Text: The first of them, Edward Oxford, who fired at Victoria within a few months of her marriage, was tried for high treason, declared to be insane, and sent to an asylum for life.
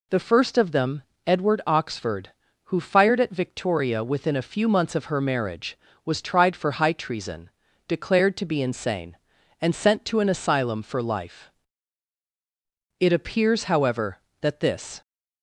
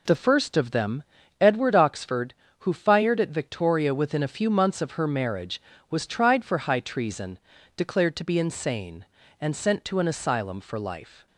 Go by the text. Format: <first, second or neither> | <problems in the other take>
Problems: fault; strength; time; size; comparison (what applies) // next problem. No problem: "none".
second | goes on to say "It appears however that this"; strong; from 12.9 s on; 2.0 s long